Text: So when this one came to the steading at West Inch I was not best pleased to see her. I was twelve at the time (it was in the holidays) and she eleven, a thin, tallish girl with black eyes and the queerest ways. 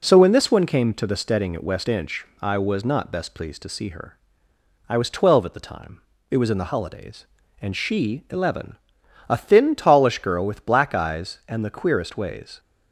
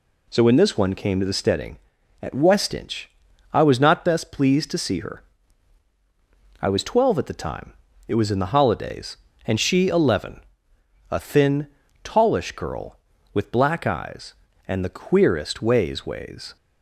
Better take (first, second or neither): first